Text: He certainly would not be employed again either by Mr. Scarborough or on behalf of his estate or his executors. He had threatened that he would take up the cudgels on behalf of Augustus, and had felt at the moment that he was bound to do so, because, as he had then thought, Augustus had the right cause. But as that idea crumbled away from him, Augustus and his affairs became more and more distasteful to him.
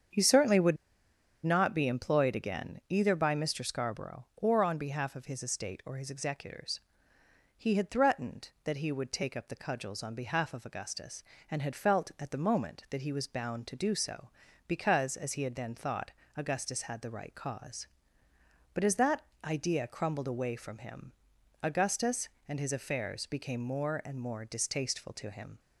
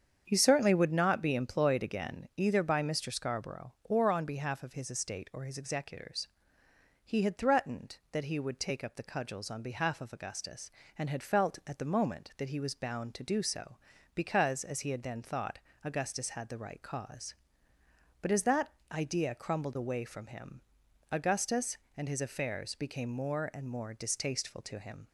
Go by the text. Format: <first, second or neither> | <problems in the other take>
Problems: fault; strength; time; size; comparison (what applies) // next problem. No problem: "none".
second | starts louder than the rest; strong; until 1.8 s; 7.5 dB; strong in the second // pauses between "would" and "not"; noticeable; at 0.7 s; 0.68 s long // pauses between "that" and "idea"; slight; at 19.2 s; 0.18 s long; slight in the second